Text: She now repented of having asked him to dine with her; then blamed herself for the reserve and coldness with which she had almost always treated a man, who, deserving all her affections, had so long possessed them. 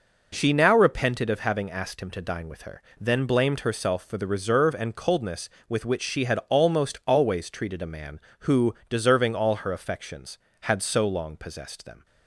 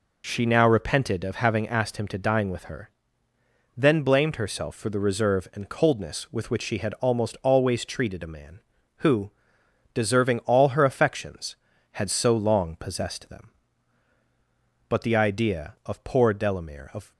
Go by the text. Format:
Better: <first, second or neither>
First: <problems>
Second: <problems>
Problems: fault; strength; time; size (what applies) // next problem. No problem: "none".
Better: first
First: none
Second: goes on to say "But the idea of poor Delamere of"; strong; from 14.8 s on; 2.2 s long